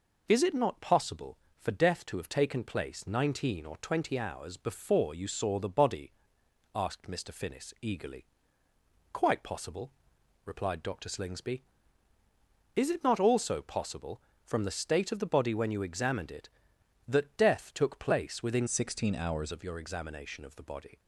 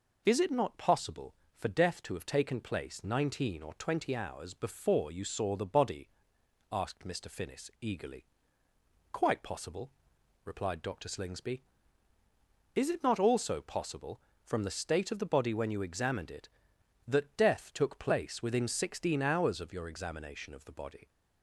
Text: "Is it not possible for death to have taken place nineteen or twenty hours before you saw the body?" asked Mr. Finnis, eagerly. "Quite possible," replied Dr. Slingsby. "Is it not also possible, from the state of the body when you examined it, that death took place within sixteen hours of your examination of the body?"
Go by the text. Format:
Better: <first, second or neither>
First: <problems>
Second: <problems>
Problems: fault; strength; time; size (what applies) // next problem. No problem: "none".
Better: second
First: changes voice from "sixteen" to "hours"; from 18.6 to 19.5 s; 0.9 s long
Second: none